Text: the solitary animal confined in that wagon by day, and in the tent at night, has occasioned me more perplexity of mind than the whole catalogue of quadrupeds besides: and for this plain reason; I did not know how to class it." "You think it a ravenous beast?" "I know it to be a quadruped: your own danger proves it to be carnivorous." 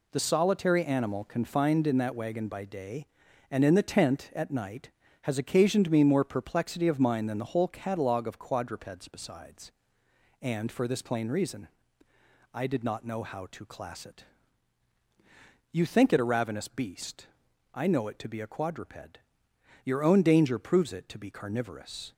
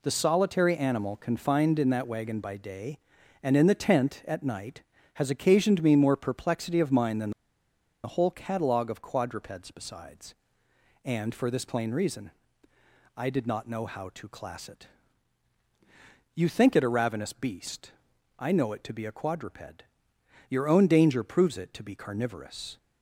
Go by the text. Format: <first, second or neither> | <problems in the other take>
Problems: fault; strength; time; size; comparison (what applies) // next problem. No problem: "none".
first | pauses between "than" and "the"; noticeable; at 7.3 s; 0.73 s long